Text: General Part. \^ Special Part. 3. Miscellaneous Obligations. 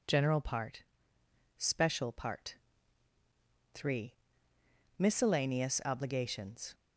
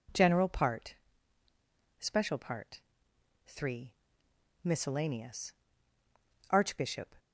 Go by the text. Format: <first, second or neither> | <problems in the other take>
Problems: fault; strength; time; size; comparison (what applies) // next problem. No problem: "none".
first | says "Archbishop" for "Obligations"; at 6.4 s